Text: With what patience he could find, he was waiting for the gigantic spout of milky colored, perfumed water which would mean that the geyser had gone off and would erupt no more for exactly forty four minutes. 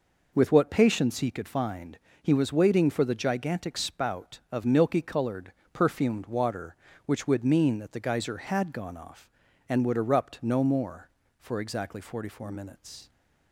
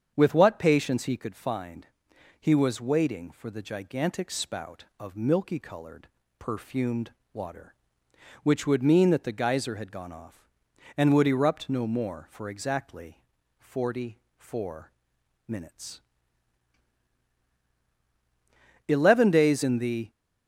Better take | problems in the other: first | starts louder than the rest; strong; until 1.1 s; 7.5 dB // pauses between "perfumed" and "water"; slight; at 7.1 s; 0.22 s long // pauses between "exactly" and "forty"; at 13.2 s; 0.38 s long // pauses between "forty" and "four"; slight; at 14.1 s; 0.20 s long // pauses between "four" and "minutes"; noticeable; at 14.9 s; 0.57 s long // goes on to say "Eleven days in the"; noticeable; from 18.8 s on; 1.2 s long

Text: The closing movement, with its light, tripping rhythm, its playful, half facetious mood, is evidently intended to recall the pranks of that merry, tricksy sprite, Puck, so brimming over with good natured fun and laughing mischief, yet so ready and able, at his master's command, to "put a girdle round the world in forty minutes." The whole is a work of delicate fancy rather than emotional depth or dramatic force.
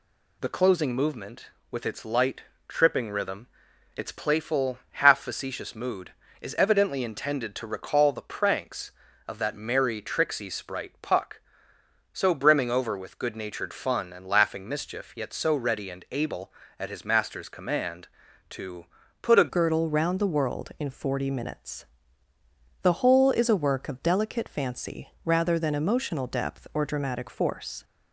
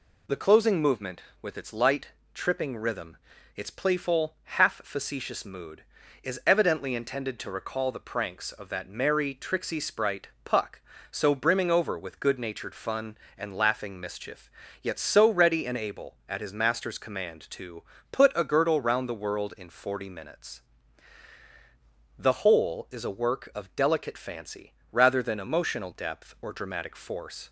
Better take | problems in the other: second | pauses between "to" and "put"; slight; at 18.8 s; 0.36 s long; slight in the second // changes voice at "girdle"; from 19.4 s on; 8.4 s long // pauses between "fancy" and "rather"; slight; at 25.0 s; 0.16 s long; slight in the second

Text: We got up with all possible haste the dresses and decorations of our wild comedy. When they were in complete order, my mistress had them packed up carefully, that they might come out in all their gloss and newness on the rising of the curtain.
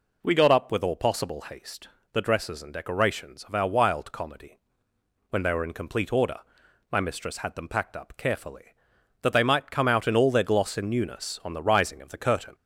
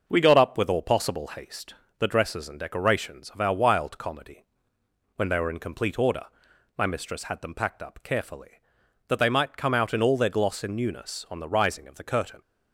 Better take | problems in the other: first | gets quieter; slight; throughout; 3 dB // pauses between "haste" and "the"; slight; at 1.7 s; 0.24 s long; slight in the first

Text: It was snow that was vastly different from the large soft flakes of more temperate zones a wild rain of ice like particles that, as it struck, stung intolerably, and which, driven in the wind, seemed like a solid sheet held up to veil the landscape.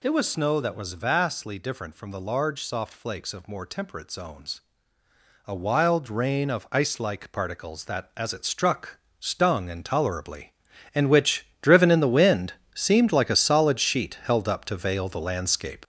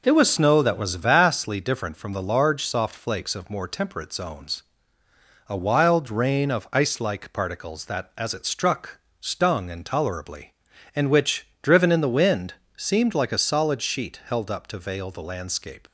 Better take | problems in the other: second | gets louder; throughout; 6 dB // pauses between "zones" and "a"; noticeable; at 4.6 s; 0.86 s long; noticeable in the second

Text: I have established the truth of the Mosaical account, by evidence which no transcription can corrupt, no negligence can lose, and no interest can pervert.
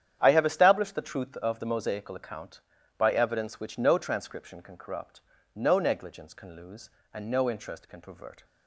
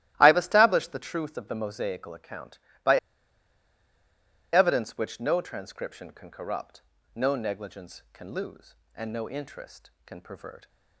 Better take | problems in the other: first | starts louder than the rest; strong; until 1.1 s; 14.5 dB; strong in the first // pauses between "by" and "evidence"; strong; at 2.9 s; 1.5 s long

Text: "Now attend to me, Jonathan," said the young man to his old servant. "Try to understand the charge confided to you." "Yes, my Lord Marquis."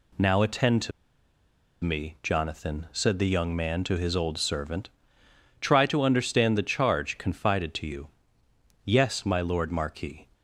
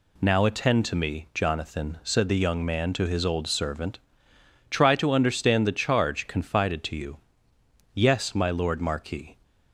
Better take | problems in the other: second | pauses between "to" and "me"; noticeable; at 0.9 s; 0.92 s long

